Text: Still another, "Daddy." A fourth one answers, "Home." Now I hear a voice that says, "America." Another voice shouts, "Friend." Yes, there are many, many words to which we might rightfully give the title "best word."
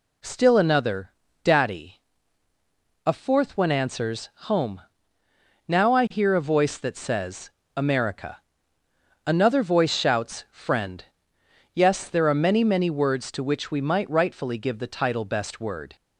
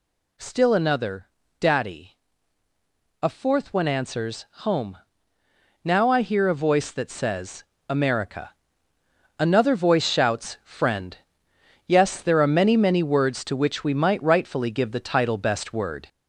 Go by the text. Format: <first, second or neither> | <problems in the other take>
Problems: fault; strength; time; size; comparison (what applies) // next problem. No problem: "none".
first | gets louder; slight; throughout; 3 dB